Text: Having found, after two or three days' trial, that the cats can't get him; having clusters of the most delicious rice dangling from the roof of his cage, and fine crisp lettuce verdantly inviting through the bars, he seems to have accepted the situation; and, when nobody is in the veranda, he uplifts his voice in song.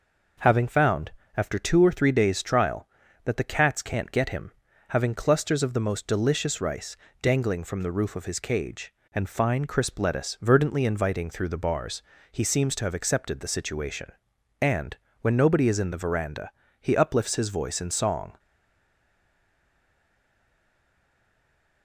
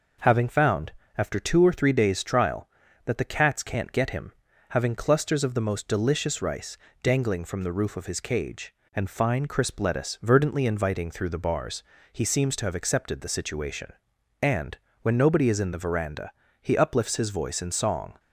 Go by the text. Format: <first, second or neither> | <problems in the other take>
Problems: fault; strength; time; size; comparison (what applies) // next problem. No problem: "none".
second | pauses between "rice" and "dangling"; slight; at 6.9 s; 0.24 s long; slight in the second // stays silent after the last word; strong; from 18.3 s on; 3.5 s long